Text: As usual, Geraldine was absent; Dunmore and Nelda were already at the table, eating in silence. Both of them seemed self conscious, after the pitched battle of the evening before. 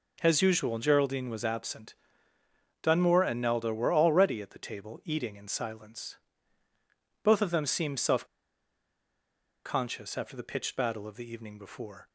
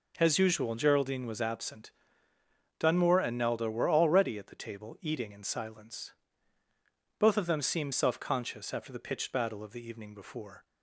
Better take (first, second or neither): second